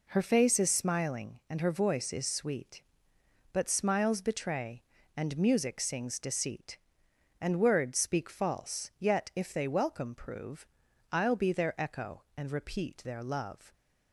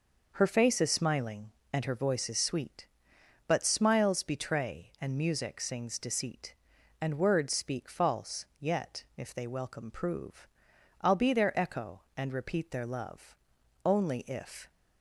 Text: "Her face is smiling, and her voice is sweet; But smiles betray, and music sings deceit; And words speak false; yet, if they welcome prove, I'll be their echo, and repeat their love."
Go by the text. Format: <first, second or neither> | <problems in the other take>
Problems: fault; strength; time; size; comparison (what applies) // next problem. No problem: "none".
first | goes on to say "Only if"; noticeable; from 13.8 s on; 0.86 s long